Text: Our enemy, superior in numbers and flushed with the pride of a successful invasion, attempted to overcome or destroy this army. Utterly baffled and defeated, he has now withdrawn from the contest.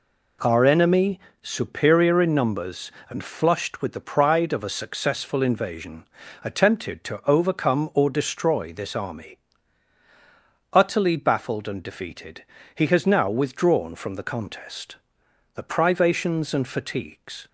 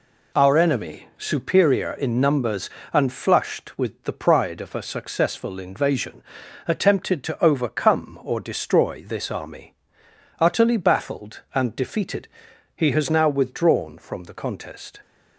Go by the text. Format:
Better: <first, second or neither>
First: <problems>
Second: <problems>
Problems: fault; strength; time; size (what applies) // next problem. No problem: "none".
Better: second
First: goes on to say "The privations and fatigues"; strong; from 15.5 s on; 1.9 s long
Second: none